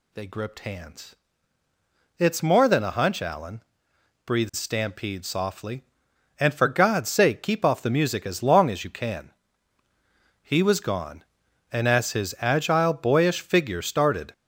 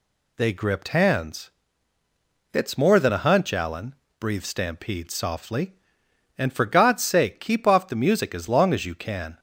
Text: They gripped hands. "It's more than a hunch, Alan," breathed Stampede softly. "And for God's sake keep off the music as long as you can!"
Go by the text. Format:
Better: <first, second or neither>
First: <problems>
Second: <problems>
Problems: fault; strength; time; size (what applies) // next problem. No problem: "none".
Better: second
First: goes on to say "He was gone and as his agile boyish figure started"; strong; from 10.4 s on; 3.9 s long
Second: none